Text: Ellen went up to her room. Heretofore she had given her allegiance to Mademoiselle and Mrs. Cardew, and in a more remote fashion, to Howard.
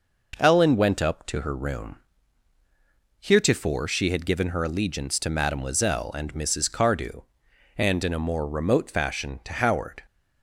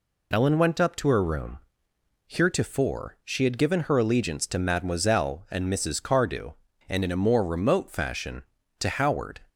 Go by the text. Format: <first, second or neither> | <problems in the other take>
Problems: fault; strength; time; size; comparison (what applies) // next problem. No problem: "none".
neither | none